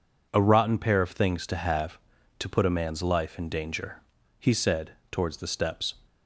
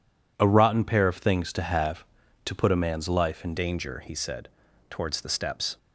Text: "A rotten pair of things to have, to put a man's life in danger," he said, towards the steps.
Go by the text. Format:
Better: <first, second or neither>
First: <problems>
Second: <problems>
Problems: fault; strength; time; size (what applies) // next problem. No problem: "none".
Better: first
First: none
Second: changes voice at "danger"; from 3.5 s on; 2.2 s long